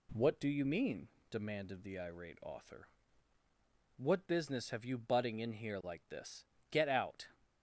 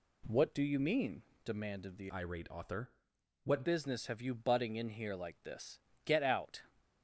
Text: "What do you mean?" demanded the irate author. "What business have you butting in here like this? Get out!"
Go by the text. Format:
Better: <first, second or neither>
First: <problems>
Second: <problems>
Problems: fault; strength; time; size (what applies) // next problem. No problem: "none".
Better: first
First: none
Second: changes voice from "irate" to "What"; from 2.1 to 3.6 s; 1.5 s long